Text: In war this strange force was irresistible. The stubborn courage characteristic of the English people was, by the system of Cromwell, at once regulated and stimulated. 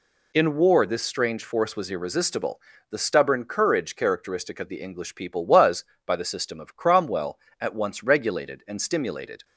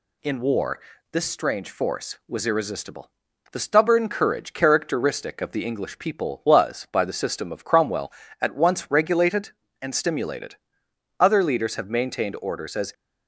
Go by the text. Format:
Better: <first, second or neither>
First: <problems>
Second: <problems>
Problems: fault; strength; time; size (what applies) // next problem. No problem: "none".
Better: first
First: none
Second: pauses between "war" and "this"; slight; at 0.8 s; 0.32 s long // goes on to say "Other leaders have maintained orders as"; strong; from 11.1 s on; 1.7 s long